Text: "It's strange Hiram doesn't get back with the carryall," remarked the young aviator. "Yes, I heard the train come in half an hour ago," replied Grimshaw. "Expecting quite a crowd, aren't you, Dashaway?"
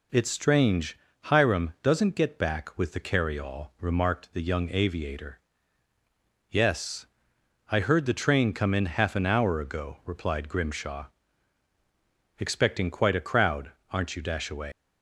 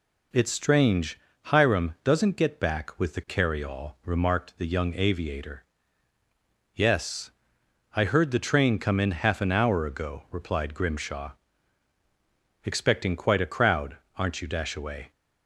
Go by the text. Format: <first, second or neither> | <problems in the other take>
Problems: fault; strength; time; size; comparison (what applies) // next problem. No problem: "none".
second | pauses between "strange" and "Hiram"; slight; at 0.9 s; 0.28 s long; slight in the second // leaves "Dashaway" unfinished; at 14.7 s; 125 ms